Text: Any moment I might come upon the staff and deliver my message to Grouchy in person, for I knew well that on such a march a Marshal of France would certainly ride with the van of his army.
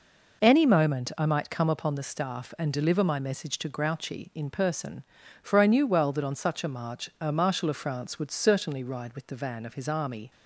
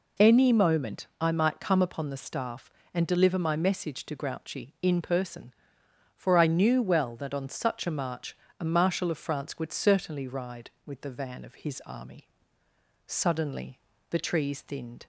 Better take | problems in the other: first | pauses between "march" and "a"; slight; at 8.3 s; 0.24 s long // goes on to say "Suddenly the trees thinned"; strong; from 13.0 s on; 2.0 s long

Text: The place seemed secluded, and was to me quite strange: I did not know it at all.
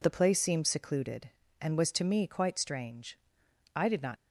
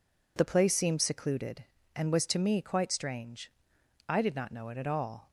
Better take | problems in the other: second | stops before "know it at all"; at 4.1 s

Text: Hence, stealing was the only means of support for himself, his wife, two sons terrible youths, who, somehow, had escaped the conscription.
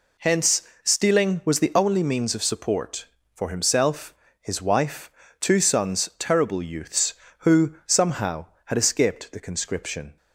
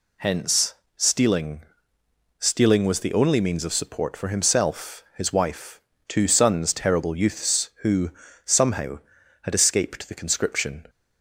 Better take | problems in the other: first | says "stealing" twice; at 2.3 s

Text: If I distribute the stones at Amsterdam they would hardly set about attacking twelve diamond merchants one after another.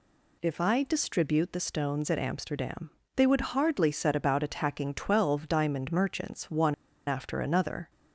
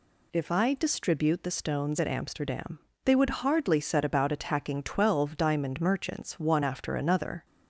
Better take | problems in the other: second | pauses between "Amsterdam" and "they"; slight; at 2.9 s; 0.26 s long; slight in the second // pauses between "one" and "after"; slight; at 6.7 s; 0.35 s long

